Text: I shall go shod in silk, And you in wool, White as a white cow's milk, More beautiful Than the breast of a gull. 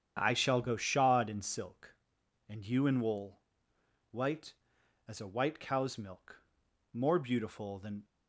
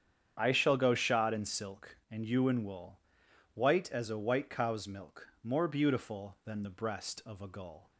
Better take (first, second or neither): second